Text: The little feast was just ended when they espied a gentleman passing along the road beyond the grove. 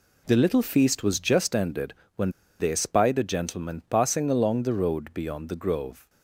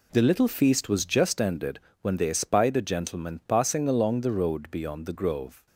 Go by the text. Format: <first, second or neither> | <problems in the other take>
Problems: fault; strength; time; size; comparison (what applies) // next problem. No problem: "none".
second | pauses between "ended" and "when"; slight; at 1.9 s; 0.24 s long; slight in the second // pauses between "when" and "they"; slight; at 2.2 s; 0.30 s long